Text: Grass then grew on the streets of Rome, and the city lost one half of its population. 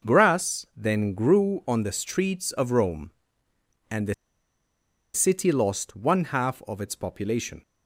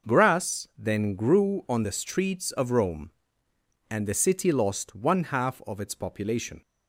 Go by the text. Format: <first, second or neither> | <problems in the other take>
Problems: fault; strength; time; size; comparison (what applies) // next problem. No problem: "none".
second | pauses between "the" and "city"; at 4.1 s; 1.0 s long